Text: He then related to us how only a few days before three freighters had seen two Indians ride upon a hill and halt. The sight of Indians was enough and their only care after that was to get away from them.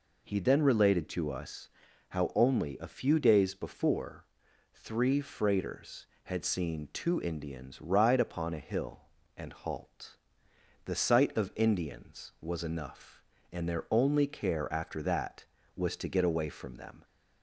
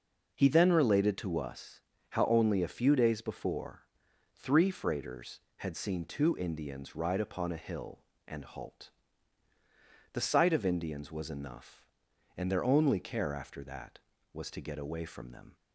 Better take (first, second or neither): neither